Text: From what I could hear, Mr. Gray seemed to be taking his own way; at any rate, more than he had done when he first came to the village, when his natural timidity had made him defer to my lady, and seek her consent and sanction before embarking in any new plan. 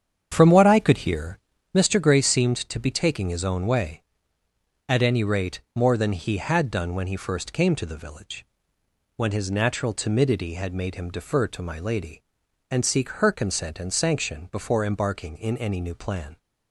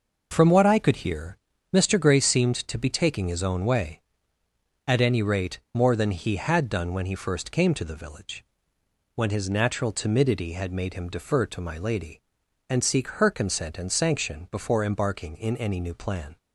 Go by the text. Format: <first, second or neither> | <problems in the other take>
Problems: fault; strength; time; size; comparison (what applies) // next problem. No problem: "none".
second | starts louder than the rest; strong; until 1.8 s; 8 dB